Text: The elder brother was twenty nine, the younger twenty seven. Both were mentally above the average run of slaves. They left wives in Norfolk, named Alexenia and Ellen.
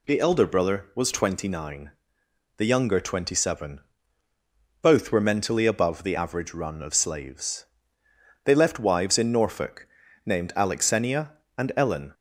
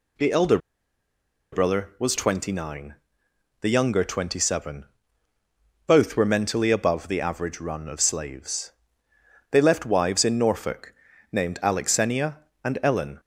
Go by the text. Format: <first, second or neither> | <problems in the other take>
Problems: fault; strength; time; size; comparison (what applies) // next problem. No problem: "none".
first | pauses between "elder" and "brother"; noticeable; at 0.5 s; 0.94 s long